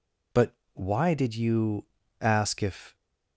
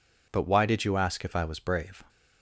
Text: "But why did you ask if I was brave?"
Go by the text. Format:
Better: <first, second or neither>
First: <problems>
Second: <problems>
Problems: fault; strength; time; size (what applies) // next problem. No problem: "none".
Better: second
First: pauses between "But" and "why"; slight; at 0.5 s; 0.20 s long // pauses between "you" and "ask"; slight; at 1.8 s; 0.36 s long // stops before "I was brave"; at 2.9 s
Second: none